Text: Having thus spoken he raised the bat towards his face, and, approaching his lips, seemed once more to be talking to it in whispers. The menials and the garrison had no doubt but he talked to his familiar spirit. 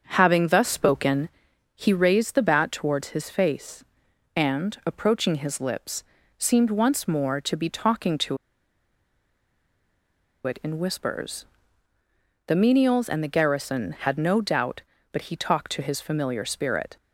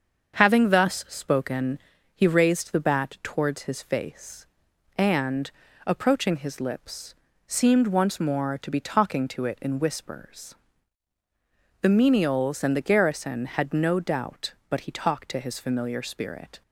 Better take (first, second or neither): second